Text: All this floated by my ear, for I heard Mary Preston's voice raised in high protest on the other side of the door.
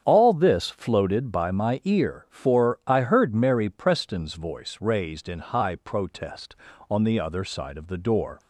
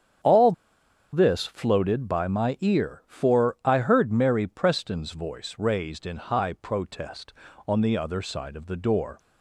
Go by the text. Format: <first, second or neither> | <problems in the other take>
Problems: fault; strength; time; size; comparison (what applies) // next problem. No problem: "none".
first | starts louder than the rest; strong; until 1.8 s; 8.5 dB; strong in the first // pauses between "All" and "this"; noticeable; at 0.5 s; 0.61 s long